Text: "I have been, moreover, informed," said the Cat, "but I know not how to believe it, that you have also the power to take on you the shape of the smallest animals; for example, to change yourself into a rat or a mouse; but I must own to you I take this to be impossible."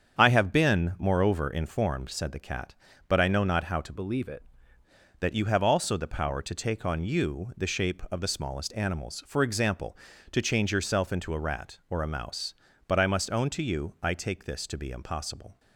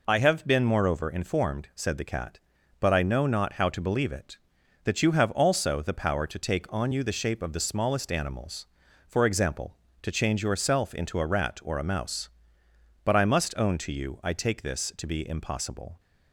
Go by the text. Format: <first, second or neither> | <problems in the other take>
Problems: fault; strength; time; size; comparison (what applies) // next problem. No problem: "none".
second | starts louder than the rest; strong; until 1.2 s; 7.5 dB // changes voice from "believe" to "it"; from 3.9 to 4.4 s; 0.5 s long